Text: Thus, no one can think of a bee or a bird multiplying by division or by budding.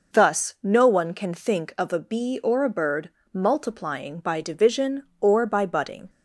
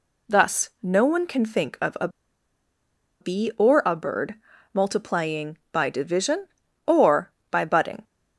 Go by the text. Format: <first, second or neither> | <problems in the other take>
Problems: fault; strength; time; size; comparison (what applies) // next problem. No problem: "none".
first | pauses between "a" and "bee"; at 2.0 s; 1.1 s long // pauses between "bird" and "multiplying"; slight; at 4.3 s; 0.36 s long; slight in the first